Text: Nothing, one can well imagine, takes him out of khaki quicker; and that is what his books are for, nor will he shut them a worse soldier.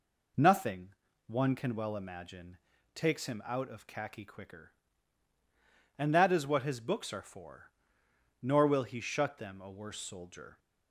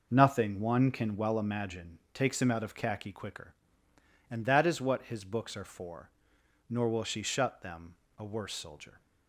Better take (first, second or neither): first